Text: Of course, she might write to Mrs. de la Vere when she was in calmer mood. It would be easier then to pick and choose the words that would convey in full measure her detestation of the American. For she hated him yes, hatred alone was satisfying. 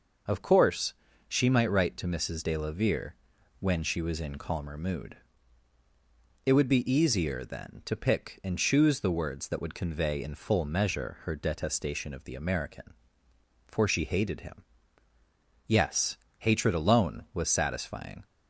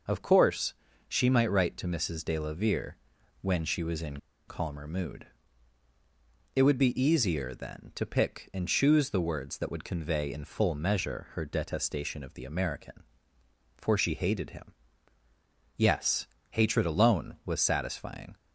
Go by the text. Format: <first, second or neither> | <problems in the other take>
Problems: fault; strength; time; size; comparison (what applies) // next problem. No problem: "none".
first | pauses between "Vere" and "when"; at 2.9 s; 0.44 s long; also in the first // pauses between "in" and "calmer"; slight; at 4.1 s; 0.31 s long // pauses between "him" and "yes"; at 14.7 s; 1.0 s long; also in the first